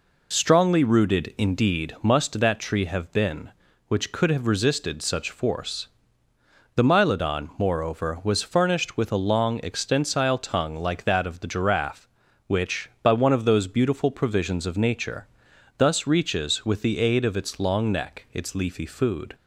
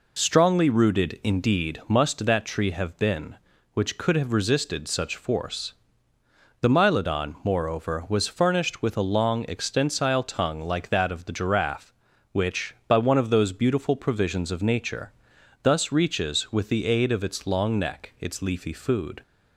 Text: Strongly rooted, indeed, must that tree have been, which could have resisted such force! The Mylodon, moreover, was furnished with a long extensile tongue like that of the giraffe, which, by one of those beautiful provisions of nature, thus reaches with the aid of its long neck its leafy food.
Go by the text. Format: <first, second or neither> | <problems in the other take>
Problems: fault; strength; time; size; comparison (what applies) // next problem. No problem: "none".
neither | none